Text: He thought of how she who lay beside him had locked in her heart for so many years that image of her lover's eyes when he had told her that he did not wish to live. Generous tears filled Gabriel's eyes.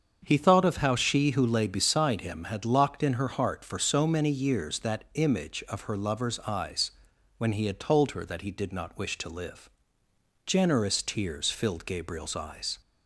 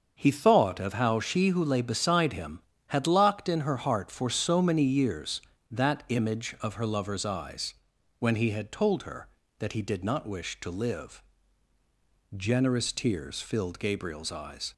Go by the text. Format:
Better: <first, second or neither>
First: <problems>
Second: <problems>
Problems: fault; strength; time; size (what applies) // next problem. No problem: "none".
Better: neither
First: starts louder than the rest; strong; until 1.2 s; 7 dB // pauses between "eyes" and "when"; noticeable; at 6.9 s; 0.46 s long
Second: starts louder than the rest; until 1.1 s; 6.5 dB // pauses between "eyes" and "when"; at 7.7 s; 0.44 s long